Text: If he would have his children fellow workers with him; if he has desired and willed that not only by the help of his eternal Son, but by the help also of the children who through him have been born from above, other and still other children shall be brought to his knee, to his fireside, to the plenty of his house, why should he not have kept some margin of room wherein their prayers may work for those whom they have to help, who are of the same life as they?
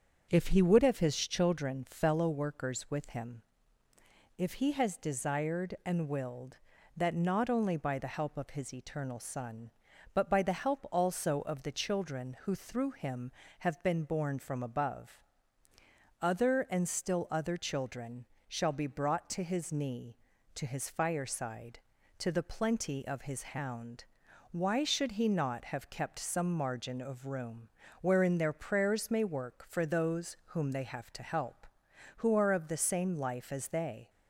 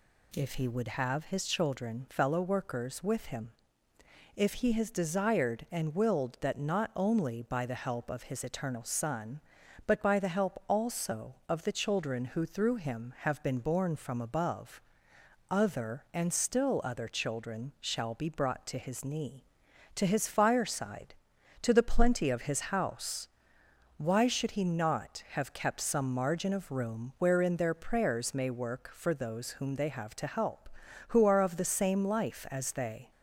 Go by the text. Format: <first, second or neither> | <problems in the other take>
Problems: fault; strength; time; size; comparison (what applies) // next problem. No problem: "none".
second | starts louder than the rest; until 1.3 s; 6.5 dB // pauses between "children" and "shall"; slight; at 18.2 s; 0.22 s long // says "hound" for "house"; at 23.4 s // pauses between "room" and "wherein"; slight; at 27.6 s; 0.34 s long